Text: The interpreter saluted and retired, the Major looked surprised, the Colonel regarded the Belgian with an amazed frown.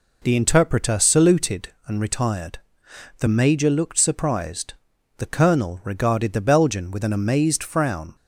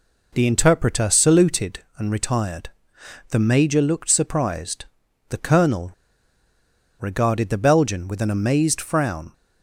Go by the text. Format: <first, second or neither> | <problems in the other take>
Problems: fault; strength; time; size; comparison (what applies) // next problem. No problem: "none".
first | pauses between "Colonel" and "regarded"; at 5.9 s; 1.0 s long